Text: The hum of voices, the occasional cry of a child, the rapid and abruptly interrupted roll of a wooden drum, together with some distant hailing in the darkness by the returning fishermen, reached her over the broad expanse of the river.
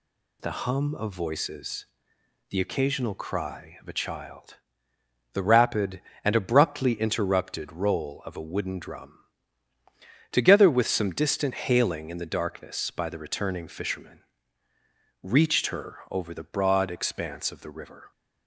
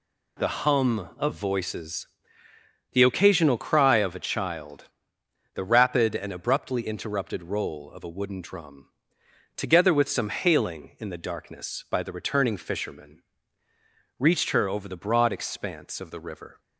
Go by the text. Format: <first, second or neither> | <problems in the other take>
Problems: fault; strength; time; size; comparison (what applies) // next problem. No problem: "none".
first | skips "distant"; at 10.2 s